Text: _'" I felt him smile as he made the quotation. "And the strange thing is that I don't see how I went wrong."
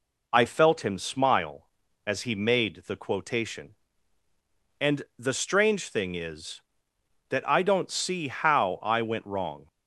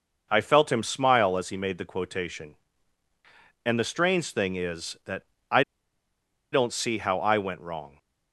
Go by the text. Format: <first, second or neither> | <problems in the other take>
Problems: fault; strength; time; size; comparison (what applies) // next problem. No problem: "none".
first | pauses between "that" and "I"; slight; at 5.2 s; 0.24 s long // pauses between "I" and "don't"; noticeable; at 5.6 s; 0.89 s long